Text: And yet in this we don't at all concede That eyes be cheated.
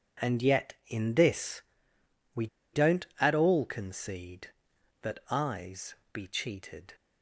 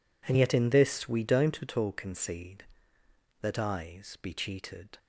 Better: second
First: pauses between "this" and "we"; noticeable; at 1.6 s; 0.72 s long // pauses between "we" and "don't"; slight; at 2.4 s; 0.26 s long // pauses between "eyes" and "be"; slight; at 5.9 s; 0.18 s long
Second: none

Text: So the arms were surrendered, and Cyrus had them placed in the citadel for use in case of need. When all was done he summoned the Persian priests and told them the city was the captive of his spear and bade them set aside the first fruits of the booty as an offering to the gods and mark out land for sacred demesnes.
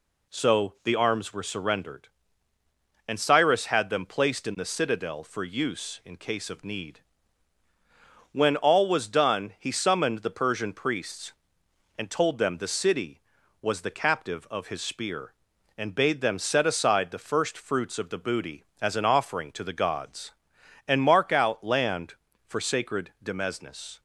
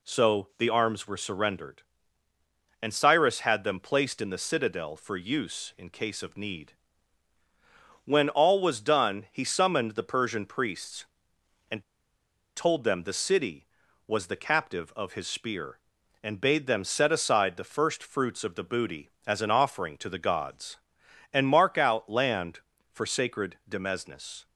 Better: first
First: none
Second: pauses between "and" and "told"; noticeable; at 11.8 s; 0.73 s long

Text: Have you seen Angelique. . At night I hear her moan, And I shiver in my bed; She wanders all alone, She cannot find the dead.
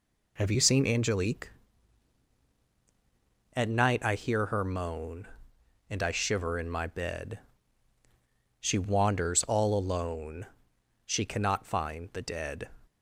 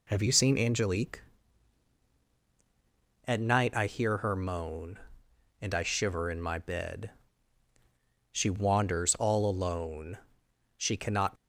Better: first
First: none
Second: stops before "find the dead"; at 11.3 s

